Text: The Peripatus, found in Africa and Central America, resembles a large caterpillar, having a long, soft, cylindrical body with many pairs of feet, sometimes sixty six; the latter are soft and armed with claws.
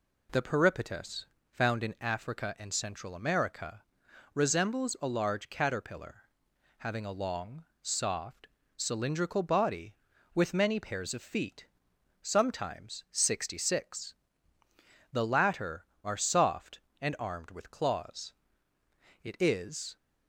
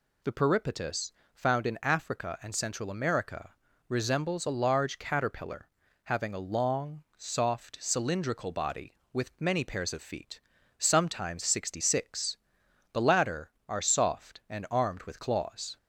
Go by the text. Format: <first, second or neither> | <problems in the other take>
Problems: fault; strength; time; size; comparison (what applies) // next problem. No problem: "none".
second | goes on to say "It is"; noticeable; from 19.2 s on; 0.72 s long